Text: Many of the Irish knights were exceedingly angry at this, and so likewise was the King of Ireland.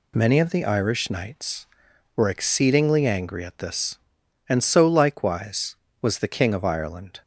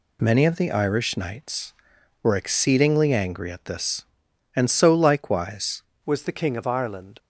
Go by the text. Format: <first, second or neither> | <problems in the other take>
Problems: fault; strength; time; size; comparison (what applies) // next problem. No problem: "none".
first | changes voice at "was"; from 6.0 s on; 1.1 s long